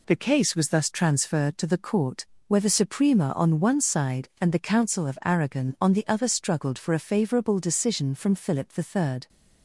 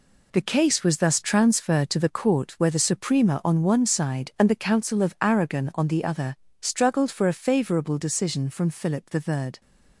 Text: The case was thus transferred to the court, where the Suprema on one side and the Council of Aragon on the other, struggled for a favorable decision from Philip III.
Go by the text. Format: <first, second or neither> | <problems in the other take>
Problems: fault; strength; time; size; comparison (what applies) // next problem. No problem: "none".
first | gets quieter; strong; throughout; 8 dB